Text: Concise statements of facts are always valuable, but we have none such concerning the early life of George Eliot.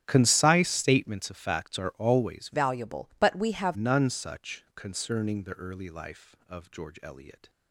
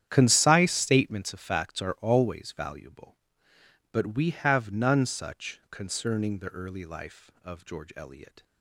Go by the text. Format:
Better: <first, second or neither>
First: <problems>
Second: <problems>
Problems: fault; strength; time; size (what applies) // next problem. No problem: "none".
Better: second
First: starts louder than the rest; strong; until 1.0 s; 9 dB // changes voice from "valuable" to "have"; from 2.5 to 3.7 s; 1.2 s long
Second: starts louder than the rest; strong; until 1.1 s; 10 dB